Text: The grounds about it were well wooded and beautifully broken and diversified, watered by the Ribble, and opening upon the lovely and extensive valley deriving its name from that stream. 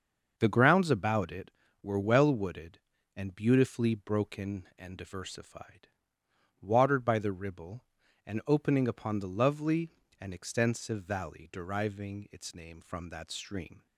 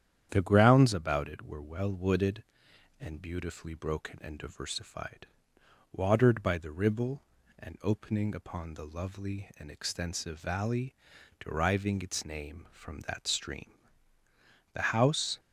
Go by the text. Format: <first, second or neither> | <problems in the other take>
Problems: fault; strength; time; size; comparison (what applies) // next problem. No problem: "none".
first | starts louder than the rest; strong; until 1.3 s; 9.5 dB; also in the first // pauses between "valley" and "deriving"; noticeable; at 10.9 s; 0.46 s long // goes on to say "The house"; noticeable; from 14.7 s on; 0.66 s long